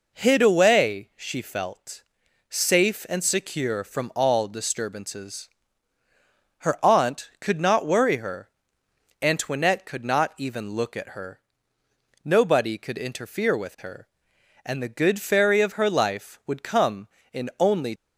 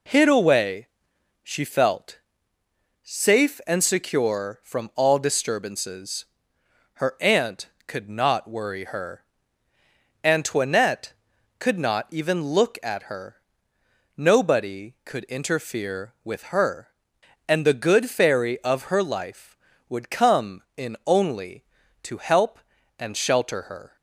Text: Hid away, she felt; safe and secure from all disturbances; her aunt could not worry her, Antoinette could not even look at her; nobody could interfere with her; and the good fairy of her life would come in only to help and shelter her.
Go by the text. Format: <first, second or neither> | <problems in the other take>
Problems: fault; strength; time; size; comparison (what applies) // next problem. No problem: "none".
second | stops before "to help and shelter her"; at 17.9 s